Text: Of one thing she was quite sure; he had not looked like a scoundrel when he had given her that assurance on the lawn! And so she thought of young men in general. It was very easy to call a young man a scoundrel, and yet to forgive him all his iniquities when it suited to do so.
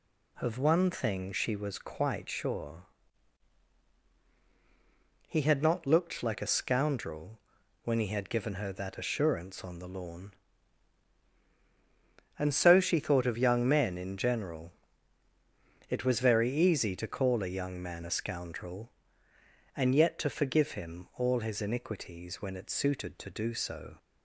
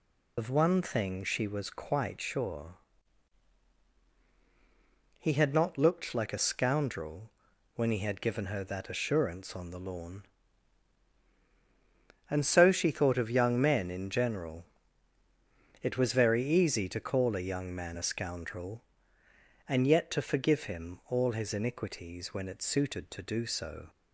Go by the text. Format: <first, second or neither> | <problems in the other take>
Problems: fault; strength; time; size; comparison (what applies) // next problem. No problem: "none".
first | loses the start of "Of"; at 0.3 s; 90 ms // pauses between "scoundrel" and "when"; noticeable; at 7.3 s; 0.46 s long; noticeable in the first